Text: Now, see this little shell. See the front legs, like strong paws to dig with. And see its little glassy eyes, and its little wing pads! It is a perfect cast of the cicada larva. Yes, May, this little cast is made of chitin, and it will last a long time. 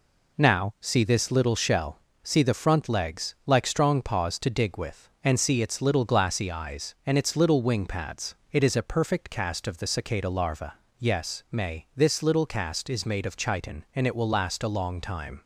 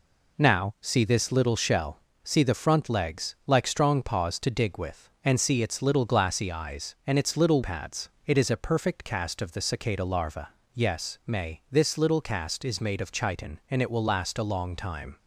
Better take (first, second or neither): first